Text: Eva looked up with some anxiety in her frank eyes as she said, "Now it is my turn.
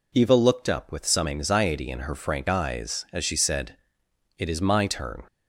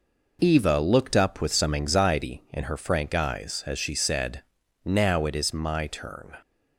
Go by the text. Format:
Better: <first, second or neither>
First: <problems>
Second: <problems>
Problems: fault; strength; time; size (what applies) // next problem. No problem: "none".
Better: second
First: skips "Now"; at 4.0 s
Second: none